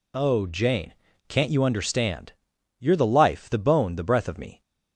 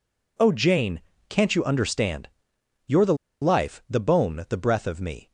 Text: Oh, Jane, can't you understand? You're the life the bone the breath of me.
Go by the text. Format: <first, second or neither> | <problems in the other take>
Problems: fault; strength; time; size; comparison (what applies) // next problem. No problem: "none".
first | pauses between "the" and "life"; slight; at 3.1 s; 0.27 s long